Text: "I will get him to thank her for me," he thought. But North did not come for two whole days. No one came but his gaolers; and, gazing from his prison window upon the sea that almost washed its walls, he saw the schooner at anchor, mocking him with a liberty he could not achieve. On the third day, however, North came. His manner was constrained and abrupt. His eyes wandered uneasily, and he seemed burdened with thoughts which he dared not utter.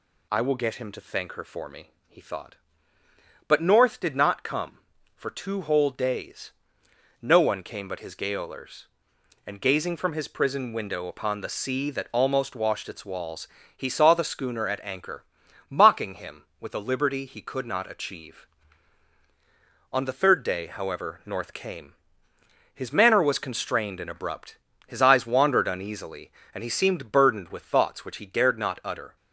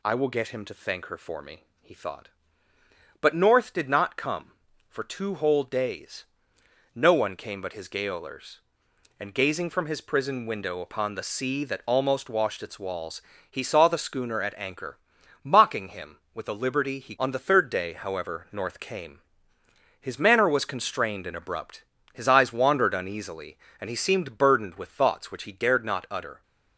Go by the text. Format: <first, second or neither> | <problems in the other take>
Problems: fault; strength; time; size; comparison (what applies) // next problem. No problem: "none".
first | skips "could not achieve"; at 17.1 s